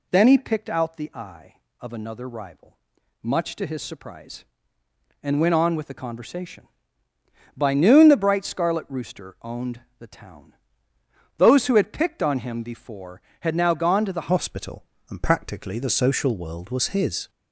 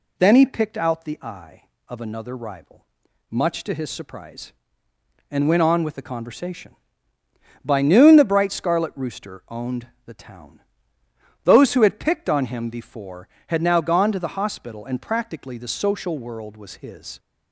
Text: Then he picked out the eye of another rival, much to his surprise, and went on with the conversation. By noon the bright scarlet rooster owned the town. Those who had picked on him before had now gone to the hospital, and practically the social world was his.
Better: second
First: pauses between "owned" and "the"; slight; at 9.7 s; 0.18 s long // changes voice at "hospital"; from 14.2 s on; 3.0 s long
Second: pauses between "owned" and "the"; slight; at 9.8 s; 0.18 s long

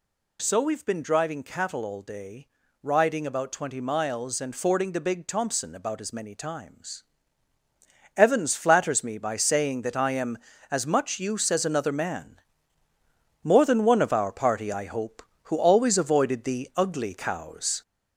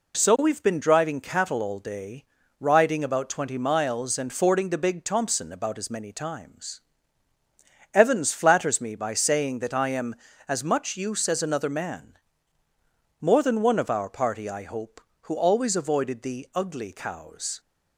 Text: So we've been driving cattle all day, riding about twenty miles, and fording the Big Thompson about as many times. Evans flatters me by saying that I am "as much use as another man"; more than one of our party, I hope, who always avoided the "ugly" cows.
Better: second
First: gets louder; throughout; 3.5 dB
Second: none

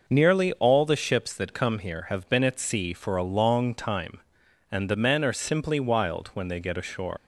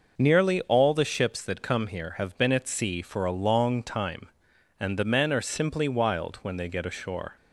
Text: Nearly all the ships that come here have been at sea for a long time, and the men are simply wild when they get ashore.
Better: second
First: leaves "ashore" unfinished; at 7.1 s; 95 ms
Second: none

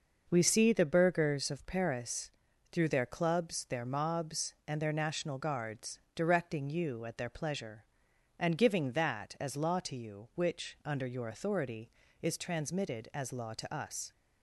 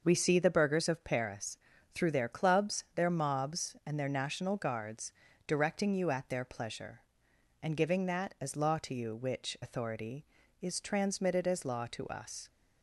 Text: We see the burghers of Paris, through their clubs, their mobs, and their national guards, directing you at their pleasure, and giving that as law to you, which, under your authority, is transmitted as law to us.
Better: first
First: none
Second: skips "under your"; at 9.5 s

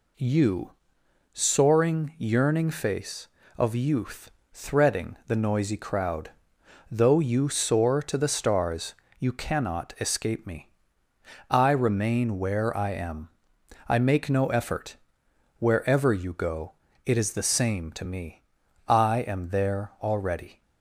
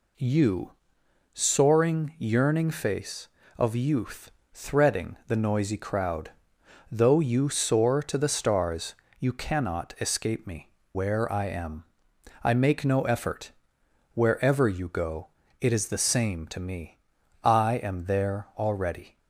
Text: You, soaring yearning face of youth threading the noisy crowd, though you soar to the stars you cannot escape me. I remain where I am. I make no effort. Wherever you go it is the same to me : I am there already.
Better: first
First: pauses between "youth" and "threading"; slight; at 4.3 s; 0.22 s long // pauses between "stars" and "you"; slight; at 8.9 s; 0.24 s long // pauses between "go" and "it"; slight; at 16.7 s; 0.32 s long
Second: pauses between "youth" and "threading"; slight; at 4.3 s; 0.22 s long // pauses between "stars" and "you"; slight; at 8.9 s; 0.24 s long // skips "I remain"; at 10.8 s // pauses between "go" and "it"; slight; at 15.2 s; 0.32 s long

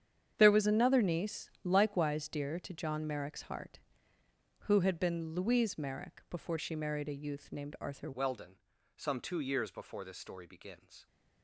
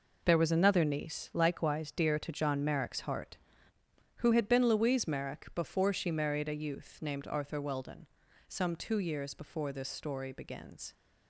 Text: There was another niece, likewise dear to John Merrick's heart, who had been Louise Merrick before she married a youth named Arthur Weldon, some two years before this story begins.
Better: second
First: starts louder than the rest; strong; until 1.3 s; 8.5 dB // changes voice at "Weldon"; from 8.1 s on; 2.9 s long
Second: none

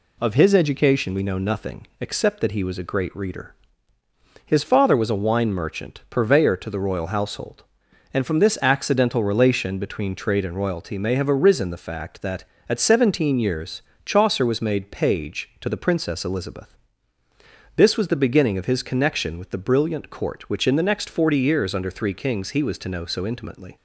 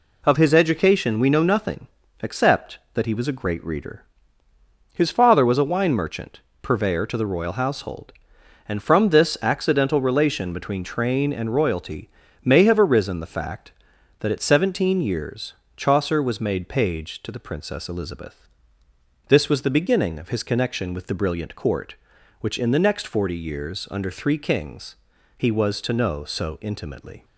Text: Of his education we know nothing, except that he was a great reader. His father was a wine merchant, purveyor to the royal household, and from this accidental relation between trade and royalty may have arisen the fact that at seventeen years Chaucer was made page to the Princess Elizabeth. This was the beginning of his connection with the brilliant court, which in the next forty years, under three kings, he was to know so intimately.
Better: first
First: pauses between "years" and "Chaucer"; slight; at 13.8 s; 0.24 s long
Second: says "train" for "trade"; at 10.8 s // pauses between "royalty" and "may"; slight; at 12.0 s; 0.36 s long // pauses between "years" and "Chaucer"; slight; at 15.5 s; 0.22 s long

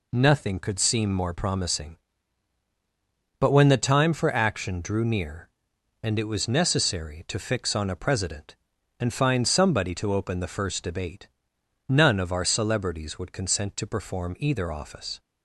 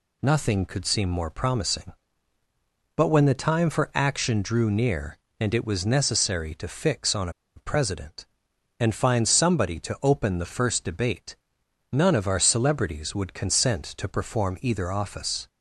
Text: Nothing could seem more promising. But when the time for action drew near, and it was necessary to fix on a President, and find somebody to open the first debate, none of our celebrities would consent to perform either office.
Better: first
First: none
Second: pauses between "on" and "a"; slight; at 7.2 s; 0.26 s long

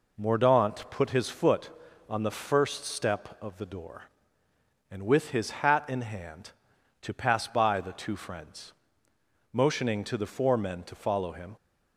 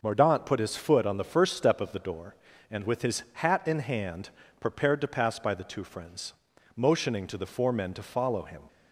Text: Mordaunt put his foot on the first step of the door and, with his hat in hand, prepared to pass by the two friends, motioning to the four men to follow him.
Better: second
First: skips "prepared"; at 6.7 s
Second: none

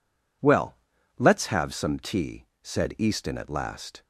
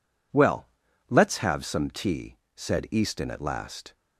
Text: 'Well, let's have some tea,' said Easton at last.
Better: neither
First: none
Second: none

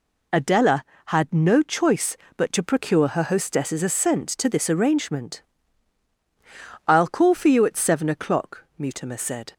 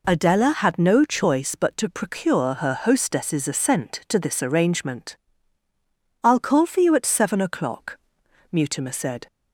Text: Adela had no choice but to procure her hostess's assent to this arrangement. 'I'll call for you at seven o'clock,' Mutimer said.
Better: neither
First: none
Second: none

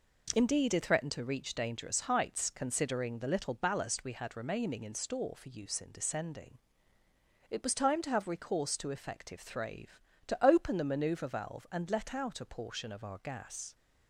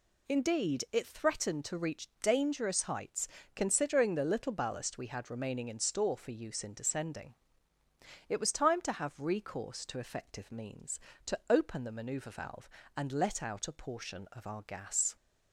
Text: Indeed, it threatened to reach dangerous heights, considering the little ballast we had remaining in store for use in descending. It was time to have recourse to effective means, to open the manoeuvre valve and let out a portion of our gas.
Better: second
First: says "thrave" for "means"; at 9.4 s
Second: none

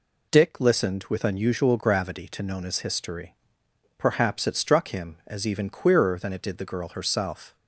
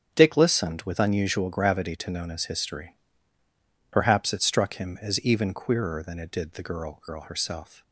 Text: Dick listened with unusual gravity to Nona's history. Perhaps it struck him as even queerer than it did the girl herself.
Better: first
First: none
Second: starts louder than the rest; strong; until 1.1 s; 8 dB // says "girl" twice; at 7.0 s

